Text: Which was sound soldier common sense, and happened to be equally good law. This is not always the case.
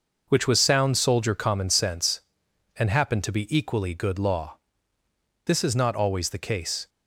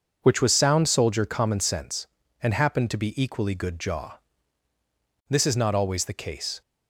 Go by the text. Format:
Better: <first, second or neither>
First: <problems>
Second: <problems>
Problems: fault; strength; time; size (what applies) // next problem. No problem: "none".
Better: first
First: none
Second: says "jaw" for "law"; at 3.7 s